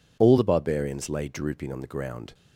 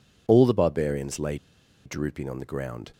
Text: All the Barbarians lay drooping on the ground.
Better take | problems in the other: first | pauses between "lay" and "drooping"; noticeable; at 1.3 s; 0.49 s long

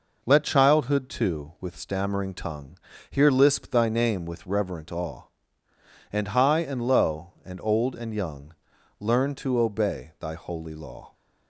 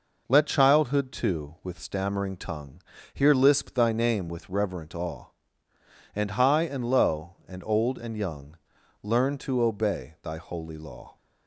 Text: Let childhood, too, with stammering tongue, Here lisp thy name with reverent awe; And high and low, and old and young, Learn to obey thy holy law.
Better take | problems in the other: neither | none

